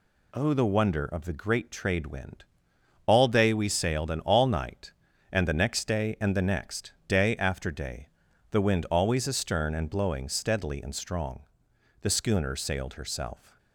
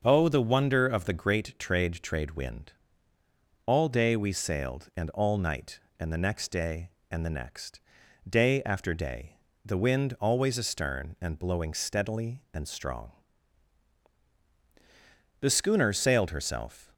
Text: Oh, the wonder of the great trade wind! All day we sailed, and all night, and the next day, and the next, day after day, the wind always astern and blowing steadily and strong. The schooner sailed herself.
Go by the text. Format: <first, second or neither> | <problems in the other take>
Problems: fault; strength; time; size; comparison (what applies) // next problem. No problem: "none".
first | starts louder than the rest; until 1.0 s; 6.5 dB // says "trade" twice; at 2.0 s